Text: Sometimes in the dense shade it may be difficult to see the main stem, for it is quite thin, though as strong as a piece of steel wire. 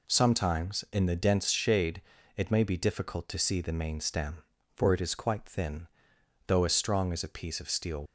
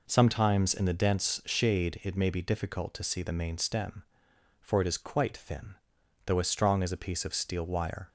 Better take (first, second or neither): second